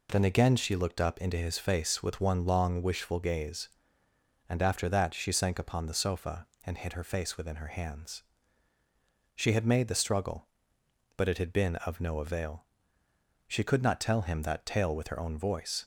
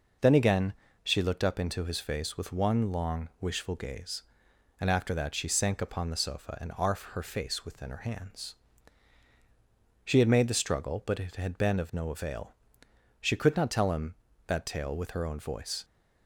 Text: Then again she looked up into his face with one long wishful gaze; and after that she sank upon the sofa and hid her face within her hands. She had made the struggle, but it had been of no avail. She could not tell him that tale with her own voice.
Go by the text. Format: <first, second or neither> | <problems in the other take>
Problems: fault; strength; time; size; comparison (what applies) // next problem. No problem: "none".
first | pauses between "again" and "she"; slight; at 0.7 s; 0.30 s long // says "arf" for "hid"; at 6.7 s